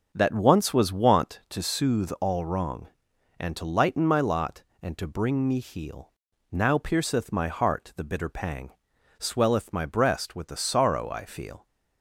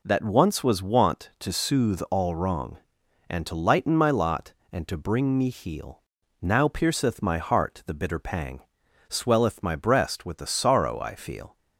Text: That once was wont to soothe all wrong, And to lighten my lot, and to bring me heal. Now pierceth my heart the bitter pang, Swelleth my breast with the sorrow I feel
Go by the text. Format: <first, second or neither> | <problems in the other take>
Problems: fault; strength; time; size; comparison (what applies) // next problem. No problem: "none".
second | starts louder than the rest; until 1.6 s; 7 dB